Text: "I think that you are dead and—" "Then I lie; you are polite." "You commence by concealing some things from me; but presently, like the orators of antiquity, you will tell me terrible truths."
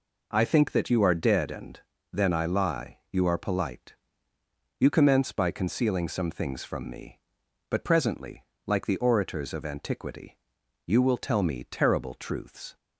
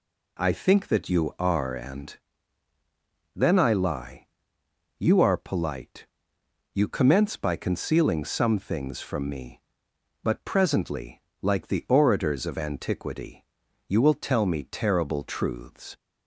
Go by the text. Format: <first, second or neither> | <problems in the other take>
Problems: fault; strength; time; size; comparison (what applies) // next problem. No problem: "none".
first | skips "dead"; at 1.7 s